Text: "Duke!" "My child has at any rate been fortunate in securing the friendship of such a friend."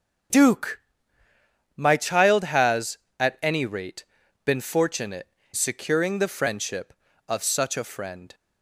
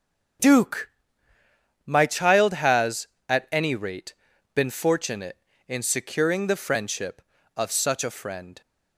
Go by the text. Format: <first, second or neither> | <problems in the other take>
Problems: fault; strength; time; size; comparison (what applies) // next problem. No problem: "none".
second | starts louder than the rest; strong; until 2.2 s; 7.5 dB; strong in the second // pauses between "rate" and "been"; at 4.0 s; 0.40 s long; also in the second // skips "in"; at 5.4 s